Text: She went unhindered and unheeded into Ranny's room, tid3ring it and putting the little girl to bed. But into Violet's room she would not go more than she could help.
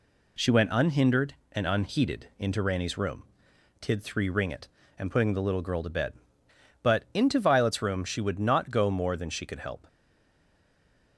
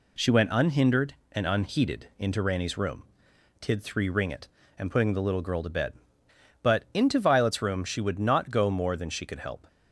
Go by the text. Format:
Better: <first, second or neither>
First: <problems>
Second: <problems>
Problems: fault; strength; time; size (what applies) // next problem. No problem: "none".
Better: second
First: stays silent after the last word; noticeable; from 9.8 s on; 1.3 s long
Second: none